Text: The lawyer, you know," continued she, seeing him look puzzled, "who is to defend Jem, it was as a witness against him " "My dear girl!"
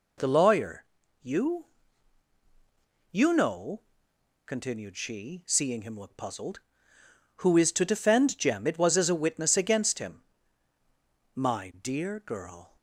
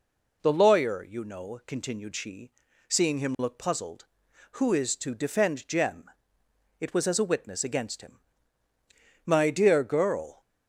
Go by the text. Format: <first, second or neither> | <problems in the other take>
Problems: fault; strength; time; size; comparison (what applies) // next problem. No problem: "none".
second | says "you" twice; at 3.1 s